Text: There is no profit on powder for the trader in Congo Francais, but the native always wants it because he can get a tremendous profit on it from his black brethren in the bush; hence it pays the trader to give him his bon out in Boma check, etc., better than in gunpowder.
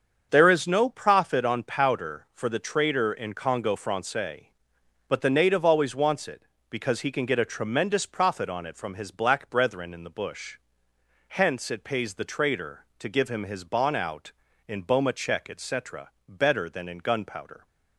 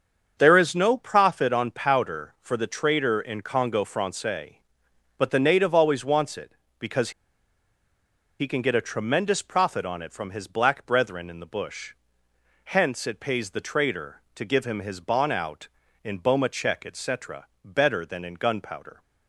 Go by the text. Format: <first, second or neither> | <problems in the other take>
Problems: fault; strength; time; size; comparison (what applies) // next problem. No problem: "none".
first | starts louder than the rest; until 1.3 s; 7 dB; also in the first // pauses between "because" and "he"; strong; at 7.1 s; 1.2 s long